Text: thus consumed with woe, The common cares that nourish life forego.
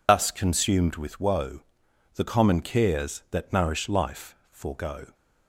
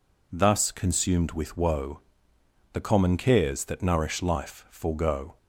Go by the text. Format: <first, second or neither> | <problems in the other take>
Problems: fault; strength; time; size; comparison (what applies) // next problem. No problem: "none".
second | loses the start of "thus"; at 0.0 s; 95 ms // pauses between "life" and "forego"; slight; at 4.3 s; 0.16 s long